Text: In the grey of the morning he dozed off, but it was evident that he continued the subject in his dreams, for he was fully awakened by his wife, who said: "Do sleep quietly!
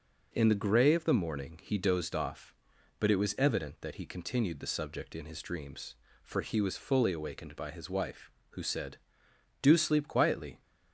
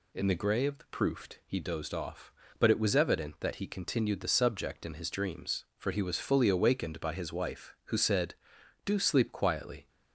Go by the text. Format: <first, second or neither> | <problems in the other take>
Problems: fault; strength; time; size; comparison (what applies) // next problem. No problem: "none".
first | says "proofed" for "morning"; at 0.8 s